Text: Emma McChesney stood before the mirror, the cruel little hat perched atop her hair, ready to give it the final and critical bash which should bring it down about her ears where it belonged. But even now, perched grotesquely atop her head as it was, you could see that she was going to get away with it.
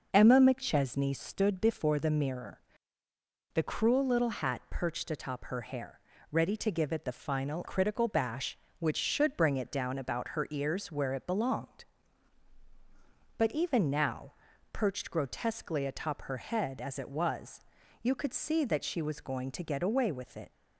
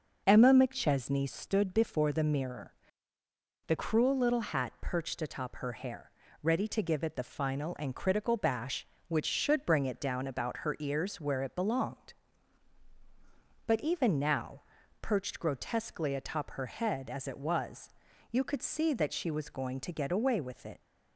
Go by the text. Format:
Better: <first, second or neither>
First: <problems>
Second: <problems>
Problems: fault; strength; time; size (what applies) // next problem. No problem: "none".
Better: second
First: skips "and"; at 7.6 s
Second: none